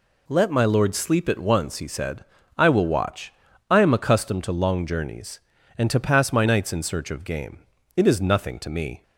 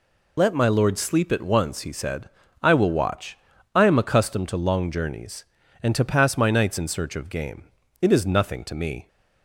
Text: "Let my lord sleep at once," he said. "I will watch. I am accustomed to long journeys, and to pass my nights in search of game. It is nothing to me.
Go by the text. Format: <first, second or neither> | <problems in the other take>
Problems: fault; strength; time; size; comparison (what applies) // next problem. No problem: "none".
first | loses the start of "Let"; at 0.3 s; 65 ms